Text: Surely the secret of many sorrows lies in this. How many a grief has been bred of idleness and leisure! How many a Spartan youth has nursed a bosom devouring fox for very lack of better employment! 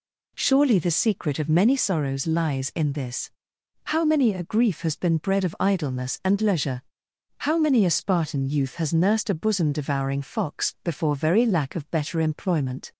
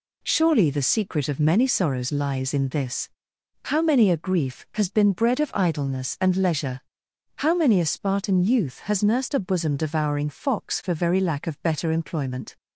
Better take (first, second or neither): second